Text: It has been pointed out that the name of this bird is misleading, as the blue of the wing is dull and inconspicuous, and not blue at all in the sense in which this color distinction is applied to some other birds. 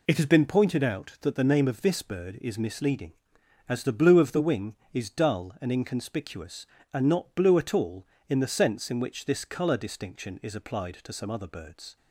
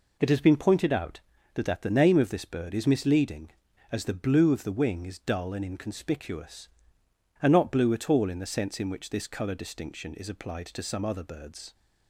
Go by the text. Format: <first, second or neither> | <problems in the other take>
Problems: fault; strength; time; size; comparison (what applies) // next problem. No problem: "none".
first | says "that" twice; at 1.6 s